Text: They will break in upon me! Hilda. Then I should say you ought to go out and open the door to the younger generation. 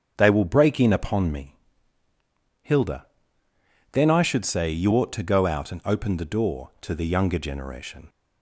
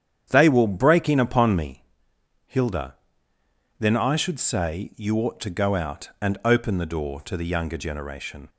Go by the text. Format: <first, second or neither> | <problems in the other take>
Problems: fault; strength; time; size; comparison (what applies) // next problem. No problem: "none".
neither | starts louder than the rest; strong; the same in both